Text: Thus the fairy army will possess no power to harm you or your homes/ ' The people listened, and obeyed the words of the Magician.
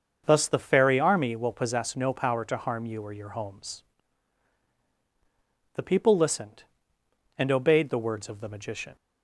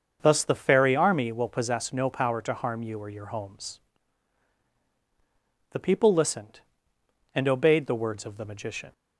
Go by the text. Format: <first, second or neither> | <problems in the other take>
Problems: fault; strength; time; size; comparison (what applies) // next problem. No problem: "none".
neither | starts louder than the rest; strong; the same in both